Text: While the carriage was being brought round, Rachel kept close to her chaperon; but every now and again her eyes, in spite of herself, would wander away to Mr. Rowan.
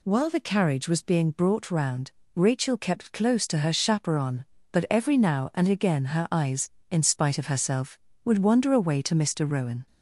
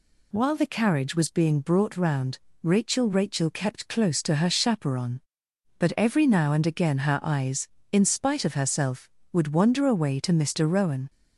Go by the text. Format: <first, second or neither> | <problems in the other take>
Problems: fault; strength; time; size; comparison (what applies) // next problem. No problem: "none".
first | says "Rachel" twice; at 3.0 s